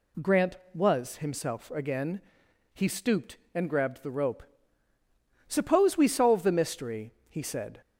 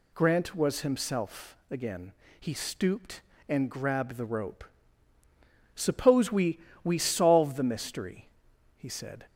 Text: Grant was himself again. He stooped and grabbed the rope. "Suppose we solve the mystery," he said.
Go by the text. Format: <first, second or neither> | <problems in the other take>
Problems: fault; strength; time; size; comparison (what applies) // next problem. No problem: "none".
first | says "we" twice; at 6.8 s